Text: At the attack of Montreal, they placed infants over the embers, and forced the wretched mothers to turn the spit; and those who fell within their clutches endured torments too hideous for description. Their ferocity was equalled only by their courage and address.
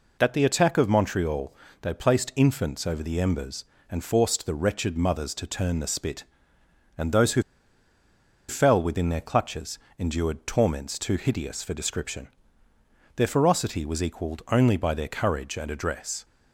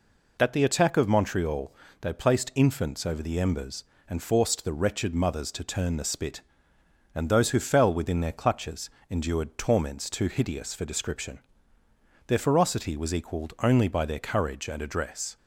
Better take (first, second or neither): second